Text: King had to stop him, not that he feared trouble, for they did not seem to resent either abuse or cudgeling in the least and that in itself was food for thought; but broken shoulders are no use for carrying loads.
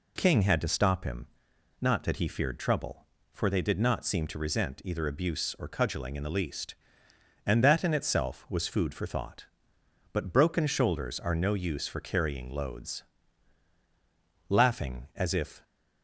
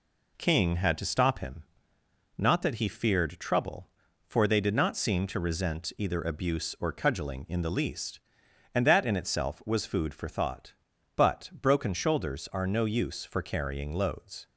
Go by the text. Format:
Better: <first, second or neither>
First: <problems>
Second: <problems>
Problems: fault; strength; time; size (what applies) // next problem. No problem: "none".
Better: second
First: goes on to say "Laughing as if"; noticeable; from 14.4 s on; 1.1 s long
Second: none